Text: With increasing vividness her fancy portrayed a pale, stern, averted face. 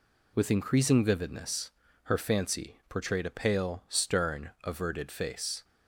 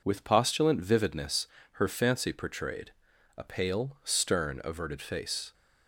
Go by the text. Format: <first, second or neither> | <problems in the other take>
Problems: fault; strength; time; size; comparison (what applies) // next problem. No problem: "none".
first | says "postulant" for "increasing"; at 0.2 s // pauses between "vividness" and "her"; slight; at 1.4 s; 0.26 s long; slight in the first // pauses between "portrayed" and "a"; noticeable; at 2.9 s; 0.46 s long